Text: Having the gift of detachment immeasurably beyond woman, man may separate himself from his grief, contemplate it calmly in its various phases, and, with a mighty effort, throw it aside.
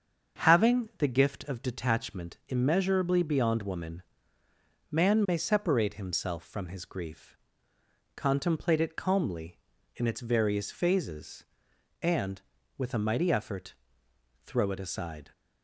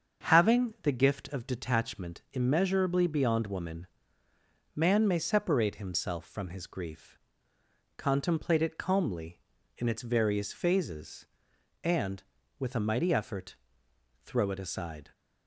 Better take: neither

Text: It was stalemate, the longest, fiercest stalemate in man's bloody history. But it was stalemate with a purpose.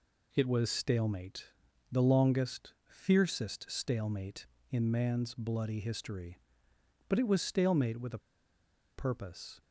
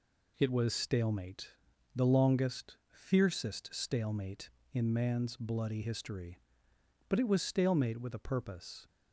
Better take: second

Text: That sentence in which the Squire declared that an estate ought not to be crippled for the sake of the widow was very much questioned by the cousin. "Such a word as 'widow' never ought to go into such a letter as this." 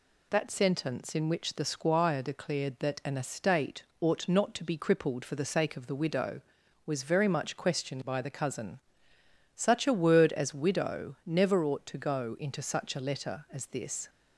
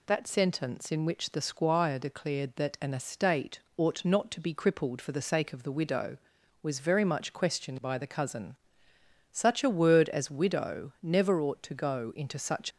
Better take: first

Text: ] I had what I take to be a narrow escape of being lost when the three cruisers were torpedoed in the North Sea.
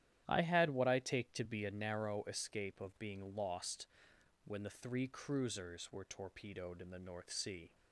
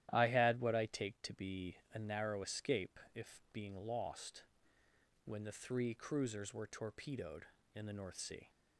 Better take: first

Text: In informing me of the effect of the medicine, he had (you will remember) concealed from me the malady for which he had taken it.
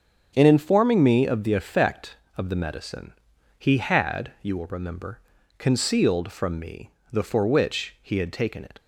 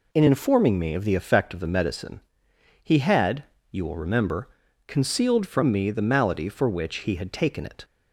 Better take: second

